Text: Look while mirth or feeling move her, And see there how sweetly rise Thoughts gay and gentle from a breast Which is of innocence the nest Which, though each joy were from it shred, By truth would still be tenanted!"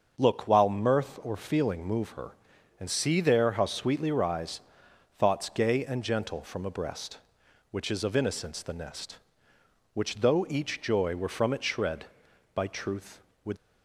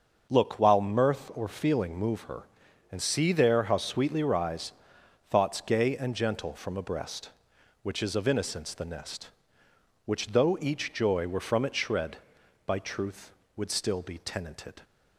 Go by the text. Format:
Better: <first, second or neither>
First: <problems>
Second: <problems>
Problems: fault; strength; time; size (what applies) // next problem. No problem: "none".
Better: second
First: starts louder than the rest; until 1.1 s; 6.5 dB // pauses between "rise" and "Thoughts"; noticeable; at 4.6 s; 0.58 s long // stops before "still be tenanted"; at 13.5 s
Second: starts louder than the rest; until 1.3 s; 6.5 dB // pauses between "rise" and "Thoughts"; noticeable; at 4.7 s; 0.58 s long